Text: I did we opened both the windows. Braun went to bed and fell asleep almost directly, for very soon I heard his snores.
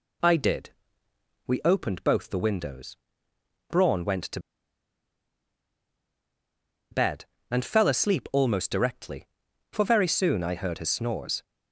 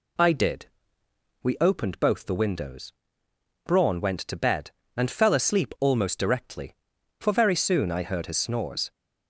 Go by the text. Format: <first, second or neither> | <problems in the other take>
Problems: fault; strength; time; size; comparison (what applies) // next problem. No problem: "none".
second | pauses between "did" and "we"; noticeable; at 0.7 s; 0.76 s long; noticeable in the second // pauses between "to" and "bed"; strong; at 4.3 s; 2.5 s long